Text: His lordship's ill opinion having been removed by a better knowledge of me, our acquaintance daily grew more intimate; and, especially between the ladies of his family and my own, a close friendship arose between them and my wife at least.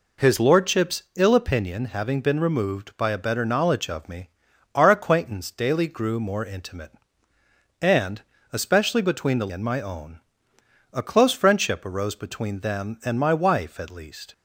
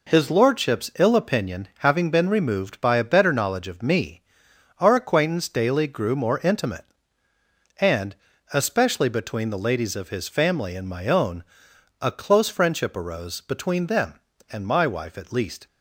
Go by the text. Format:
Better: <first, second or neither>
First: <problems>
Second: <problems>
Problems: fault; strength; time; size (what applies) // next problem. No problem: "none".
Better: second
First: skips "ladies of his family"; at 9.4 s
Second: none